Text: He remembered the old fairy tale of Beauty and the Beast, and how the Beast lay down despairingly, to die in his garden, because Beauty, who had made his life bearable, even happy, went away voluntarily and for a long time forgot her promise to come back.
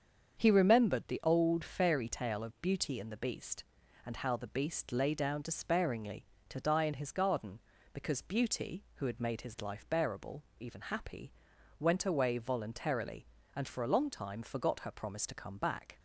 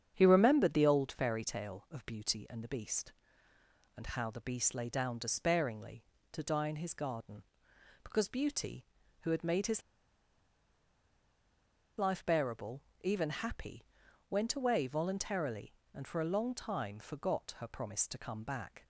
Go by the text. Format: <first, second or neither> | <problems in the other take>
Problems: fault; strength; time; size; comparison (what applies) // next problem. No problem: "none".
first | starts louder than the rest; strong; until 1.1 s; 8 dB; strong in the first // pauses between "his" and "life"; strong; at 9.8 s; 2.1 s long